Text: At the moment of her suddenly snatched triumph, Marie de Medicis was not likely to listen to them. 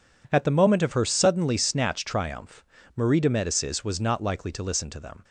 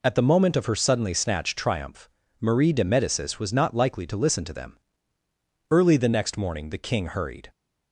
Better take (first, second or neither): first